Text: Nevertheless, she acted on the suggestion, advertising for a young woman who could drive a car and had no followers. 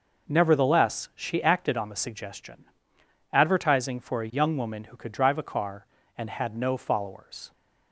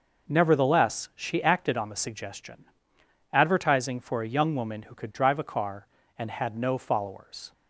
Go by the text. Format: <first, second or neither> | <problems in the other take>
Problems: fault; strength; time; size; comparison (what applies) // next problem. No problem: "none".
neither | none